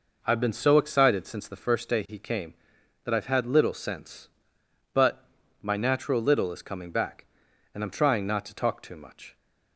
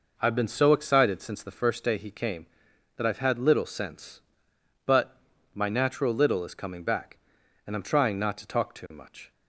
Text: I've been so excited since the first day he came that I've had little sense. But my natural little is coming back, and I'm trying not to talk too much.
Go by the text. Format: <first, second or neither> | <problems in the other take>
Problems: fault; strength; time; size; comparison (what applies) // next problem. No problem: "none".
neither | pauses between "But" and "my"; the same in both